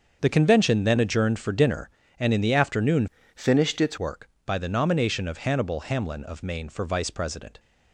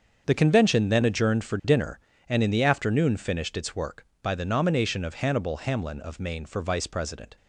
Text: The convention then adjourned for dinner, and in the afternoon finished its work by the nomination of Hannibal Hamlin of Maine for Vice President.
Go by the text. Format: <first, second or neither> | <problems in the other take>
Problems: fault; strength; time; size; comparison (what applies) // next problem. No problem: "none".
second | starts louder than the rest; until 1.2 s; 6.5 dB; also in the second // changes voice from "finished" to "its"; from 3.3 to 3.9 s; 0.6 s long